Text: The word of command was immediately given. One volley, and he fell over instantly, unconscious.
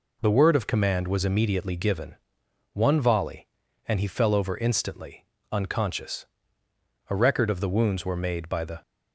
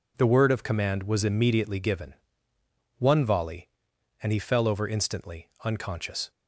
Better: second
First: goes on to say "A record of the wounds were made by the"; strong; from 7.0 s on; 1.7 s long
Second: none

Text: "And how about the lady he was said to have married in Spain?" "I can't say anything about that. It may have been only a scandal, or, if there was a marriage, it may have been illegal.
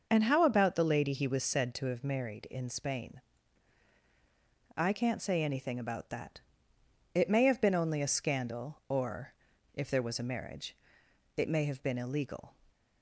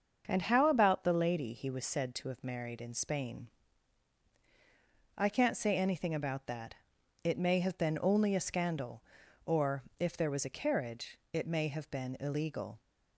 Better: first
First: starts louder than the rest; noticeable; until 1.1 s; 6 dB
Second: starts louder than the rest; until 1.2 s; 6.5 dB // says "carriage" for "marriage"; at 10.5 s

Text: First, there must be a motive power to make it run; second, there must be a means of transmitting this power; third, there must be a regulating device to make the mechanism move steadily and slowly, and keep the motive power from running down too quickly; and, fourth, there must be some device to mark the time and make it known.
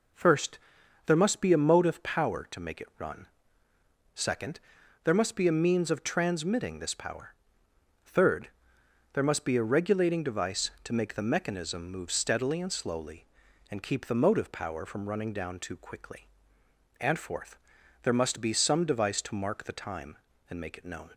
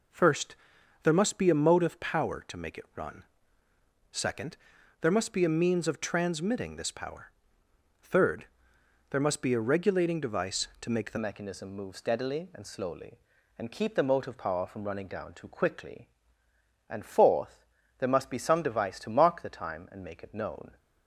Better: first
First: none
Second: changes voice at "mechanism"; from 11.1 s on; 9.6 s long

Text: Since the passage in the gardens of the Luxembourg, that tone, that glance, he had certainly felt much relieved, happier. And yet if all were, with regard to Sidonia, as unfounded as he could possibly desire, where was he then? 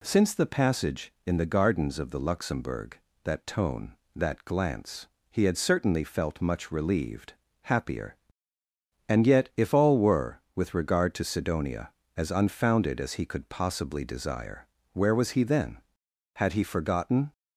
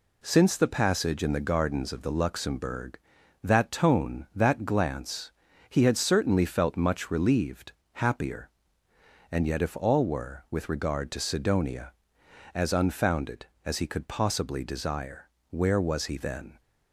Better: second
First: goes on to say "Had he forgotten"; noticeable; from 16.3 s on; 0.98 s long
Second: none

